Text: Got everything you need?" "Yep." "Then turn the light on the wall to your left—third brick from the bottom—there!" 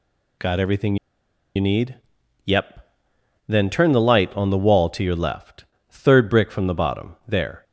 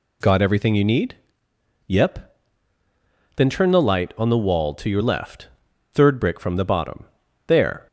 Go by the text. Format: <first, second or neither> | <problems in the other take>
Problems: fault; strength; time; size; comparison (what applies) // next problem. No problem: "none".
second | pauses between "everything" and "you"; noticeable; at 0.9 s; 0.59 s long